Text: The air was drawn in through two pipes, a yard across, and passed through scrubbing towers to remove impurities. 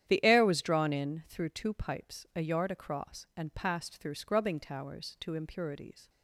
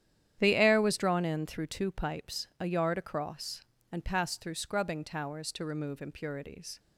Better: second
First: starts louder than the rest; strong; until 1.0 s; 10.5 dB // skips "remove"; at 5.3 s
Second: starts louder than the rest; strong; until 1.4 s; 10.5 dB

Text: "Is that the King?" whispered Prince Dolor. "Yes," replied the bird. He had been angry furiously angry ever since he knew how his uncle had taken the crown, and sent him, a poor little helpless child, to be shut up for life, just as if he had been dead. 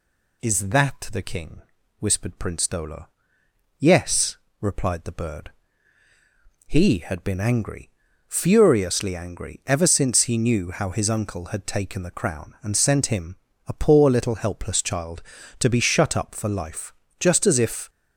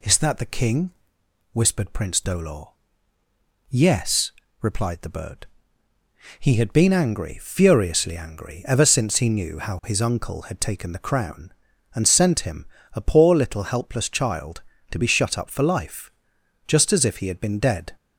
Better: second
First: pauses between "angry" and "furiously"; at 7.8 s; 0.38 s long // stops before "he had been dead"; at 17.8 s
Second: none

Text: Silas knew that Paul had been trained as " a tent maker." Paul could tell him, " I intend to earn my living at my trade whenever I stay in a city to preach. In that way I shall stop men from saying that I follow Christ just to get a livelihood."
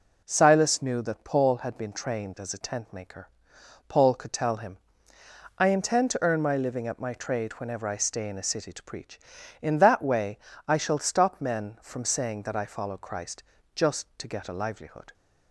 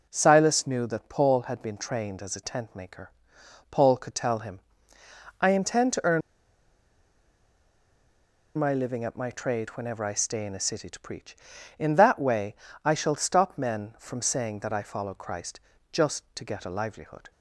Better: first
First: pauses between "way" and "I"; slight; at 10.3 s; 0.28 s long // pauses between "Christ" and "just"; slight; at 13.4 s; 0.32 s long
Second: pauses between "earn" and "my"; strong; at 6.2 s; 2.3 s long // pauses between "way" and "I"; slight; at 12.5 s; 0.28 s long // pauses between "Christ" and "just"; slight; at 15.5 s; 0.32 s long

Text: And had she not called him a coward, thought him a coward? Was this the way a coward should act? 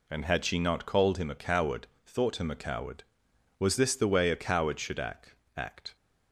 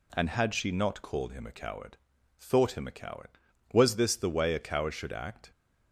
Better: second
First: says "act" twice; at 5.5 s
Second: none

